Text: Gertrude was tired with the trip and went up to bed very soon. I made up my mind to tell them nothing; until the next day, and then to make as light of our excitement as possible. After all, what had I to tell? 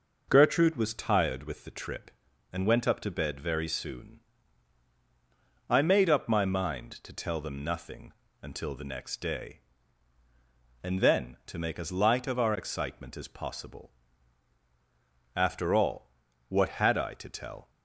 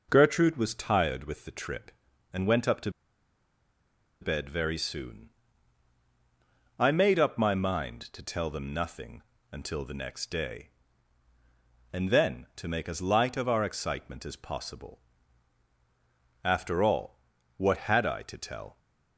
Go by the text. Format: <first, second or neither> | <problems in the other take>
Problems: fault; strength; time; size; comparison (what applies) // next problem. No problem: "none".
first | pauses between "to" and "bed"; strong; at 2.8 s; 1.3 s long